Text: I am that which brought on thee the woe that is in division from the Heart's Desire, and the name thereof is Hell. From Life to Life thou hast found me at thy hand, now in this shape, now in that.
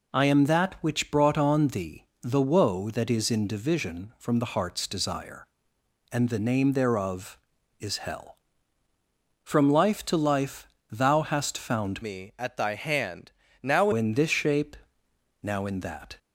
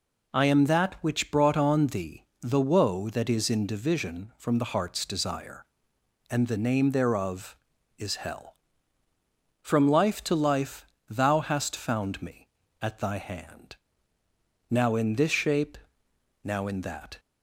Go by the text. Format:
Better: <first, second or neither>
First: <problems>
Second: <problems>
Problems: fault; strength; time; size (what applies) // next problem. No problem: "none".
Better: second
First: pauses between "thee" and "the"; slight; at 2.0 s; 0.18 s long // pauses between "Life" and "thou"; slight; at 10.6 s; 0.24 s long // changes voice from "me" to "now"; from 12.0 to 13.8 s; 1.8 s long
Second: pauses between "thee" and "the"; slight; at 2.2 s; 0.18 s long // pauses between "Life" and "thou"; slight; at 10.8 s; 0.24 s long